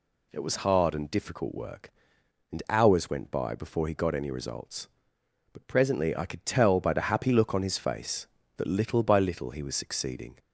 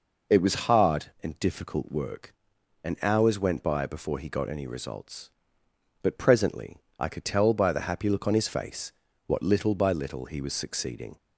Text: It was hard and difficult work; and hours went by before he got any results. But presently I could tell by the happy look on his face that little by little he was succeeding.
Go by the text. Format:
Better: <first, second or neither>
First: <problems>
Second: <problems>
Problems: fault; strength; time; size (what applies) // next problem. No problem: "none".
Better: first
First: none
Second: pauses between "presently" and "I"; slight; at 6.8 s; 0.18 s long // says "what" for "that"; at 9.2 s